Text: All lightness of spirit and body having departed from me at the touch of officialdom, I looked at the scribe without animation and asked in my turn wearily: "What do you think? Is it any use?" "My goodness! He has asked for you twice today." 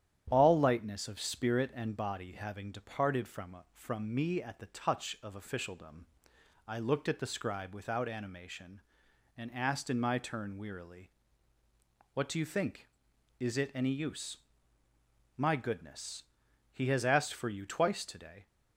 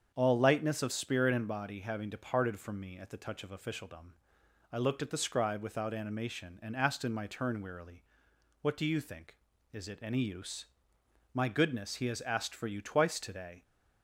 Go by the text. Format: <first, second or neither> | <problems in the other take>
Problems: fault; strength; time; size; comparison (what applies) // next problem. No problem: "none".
second | starts louder than the rest; strong; until 1.3 s; 9.5 dB; strong in the second // says "from" twice; at 3.7 s